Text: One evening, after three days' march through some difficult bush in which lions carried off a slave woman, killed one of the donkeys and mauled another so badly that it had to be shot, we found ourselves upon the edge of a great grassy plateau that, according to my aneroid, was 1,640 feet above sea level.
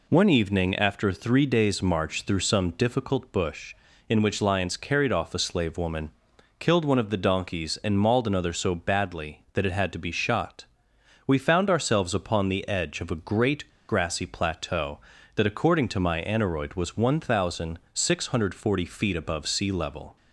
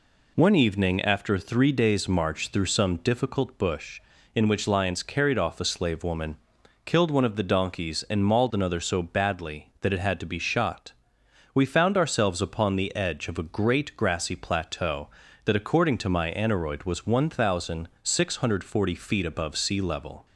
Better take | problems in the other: second | pauses between "great" and "grassy"; slight; at 13.6 s; 0.20 s long

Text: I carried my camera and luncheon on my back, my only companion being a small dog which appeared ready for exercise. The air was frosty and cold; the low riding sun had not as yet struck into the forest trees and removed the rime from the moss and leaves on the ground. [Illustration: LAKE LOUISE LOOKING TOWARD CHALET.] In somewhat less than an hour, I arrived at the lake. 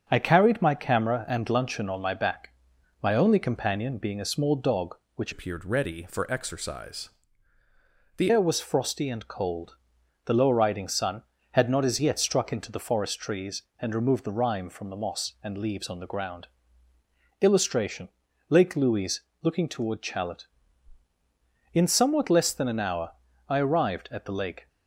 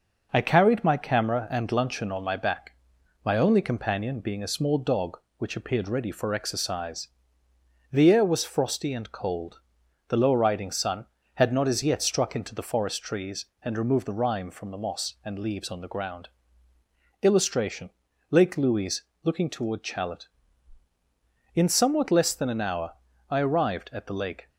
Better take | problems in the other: second | starts louder than the rest; strong; until 1.0 s; 7.5 dB // changes voice from "appeared" to "The"; from 5.3 to 8.3 s; 3.0 s long // pauses between "LOUISE" and "LOOKING"; slight; at 19.2 s; 0.20 s long; slight in the second

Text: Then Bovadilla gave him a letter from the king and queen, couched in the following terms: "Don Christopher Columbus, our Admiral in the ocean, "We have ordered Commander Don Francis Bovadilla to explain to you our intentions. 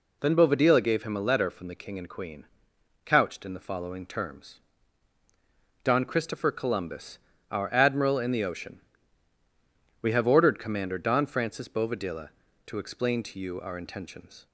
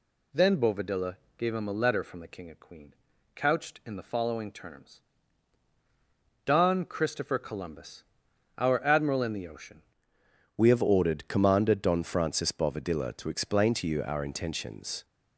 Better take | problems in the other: first | pauses between "Bovadilla" and "gave"; slight; at 1.1 s; 0.20 s long // changes voice at "We"; from 10.5 s on; 4.5 s long

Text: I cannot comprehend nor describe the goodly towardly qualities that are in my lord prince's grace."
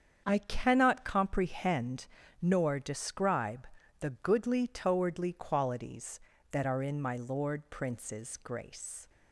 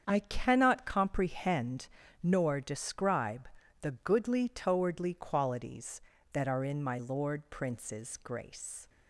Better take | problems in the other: neither | starts louder than the rest; strong; the same in both // pauses between "comprehend" and "nor"; slight; the same in both // pauses between "describe" and "the"; slight; the same in both

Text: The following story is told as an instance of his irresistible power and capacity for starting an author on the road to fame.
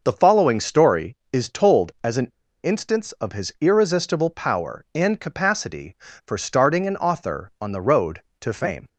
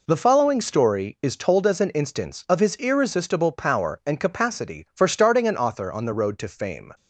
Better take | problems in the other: second | pauses between "an" and "instance"; slight; at 2.2 s; 0.33 s long

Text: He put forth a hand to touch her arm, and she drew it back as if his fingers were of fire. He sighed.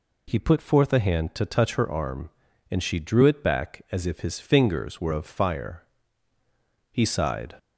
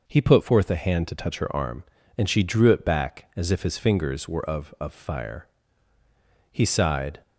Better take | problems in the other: first | says "of" twice; at 4.7 s

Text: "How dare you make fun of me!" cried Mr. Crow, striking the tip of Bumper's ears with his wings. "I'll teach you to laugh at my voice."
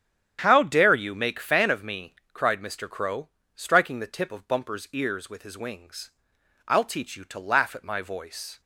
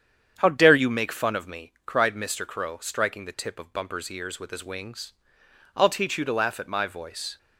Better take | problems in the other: second | starts louder than the rest; strong; until 1.4 s; 9 dB; strong in the second // says "fan" for "fun"; at 1.3 s

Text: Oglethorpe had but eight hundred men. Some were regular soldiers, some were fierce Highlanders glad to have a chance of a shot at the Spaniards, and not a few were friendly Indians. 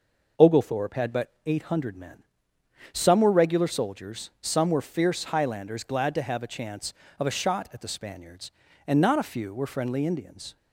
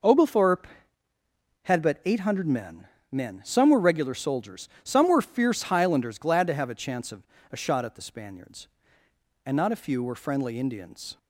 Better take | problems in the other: first | says "men" twice; at 3.1 s // pauses between "of" and "a"; slight; at 7.2 s; 0.28 s long

